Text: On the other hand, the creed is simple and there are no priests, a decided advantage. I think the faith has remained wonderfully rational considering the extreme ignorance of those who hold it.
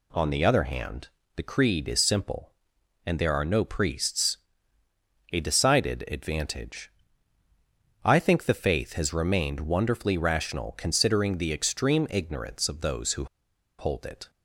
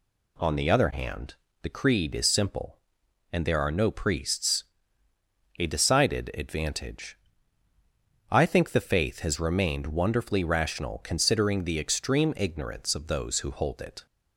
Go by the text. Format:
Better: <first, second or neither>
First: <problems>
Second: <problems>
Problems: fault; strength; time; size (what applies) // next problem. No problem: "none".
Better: second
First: pauses between "who" and "hold"; noticeable; at 13.2 s; 0.53 s long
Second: none